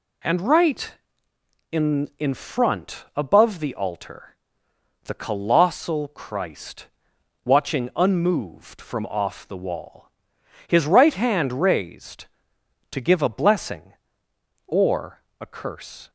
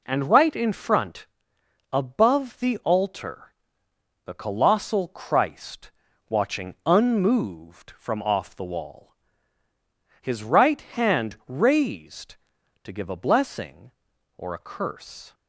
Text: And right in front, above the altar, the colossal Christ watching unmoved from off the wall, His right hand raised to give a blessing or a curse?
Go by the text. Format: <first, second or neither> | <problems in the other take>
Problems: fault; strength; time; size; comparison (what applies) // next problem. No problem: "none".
second | says "in" twice; at 2.1 s // pauses between "Christ" and "watching"; noticeable; at 6.8 s; 0.56 s long; also in the second // pauses between "or" and "a"; slight; at 15.2 s; 0.18 s long